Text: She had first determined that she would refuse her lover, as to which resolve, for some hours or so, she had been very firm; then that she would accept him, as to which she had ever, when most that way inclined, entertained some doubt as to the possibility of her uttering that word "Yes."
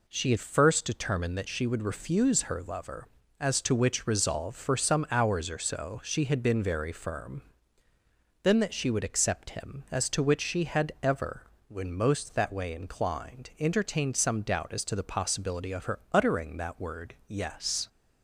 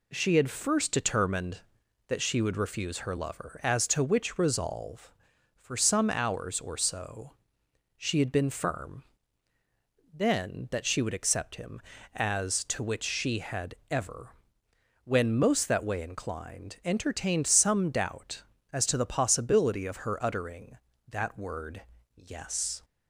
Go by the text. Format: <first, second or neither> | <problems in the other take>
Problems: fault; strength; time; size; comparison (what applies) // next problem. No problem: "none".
first | skips "very"; at 8.5 s // pauses between "had" and "ever"; slight; at 13.7 s; 0.16 s long // pauses between "word" and "Yes"; slight; at 21.8 s; 0.34 s long